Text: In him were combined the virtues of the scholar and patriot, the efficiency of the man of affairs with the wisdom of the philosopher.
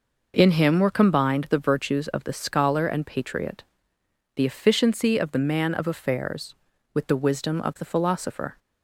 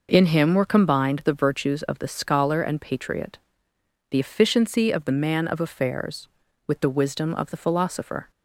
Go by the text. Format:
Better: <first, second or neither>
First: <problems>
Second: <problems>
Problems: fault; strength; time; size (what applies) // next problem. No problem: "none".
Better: neither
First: none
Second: none